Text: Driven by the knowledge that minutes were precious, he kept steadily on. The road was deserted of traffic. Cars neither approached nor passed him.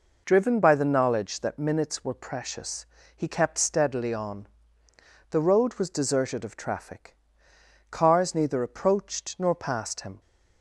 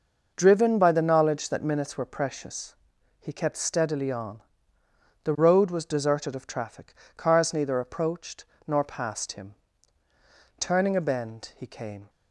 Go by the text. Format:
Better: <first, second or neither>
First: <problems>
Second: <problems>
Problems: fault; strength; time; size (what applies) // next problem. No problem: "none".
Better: first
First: none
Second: pauses between "approached" and "nor"; slight; at 8.4 s; 0.22 s long // goes on to say "Turning a bend he came"; from 10.5 s on; 1.5 s long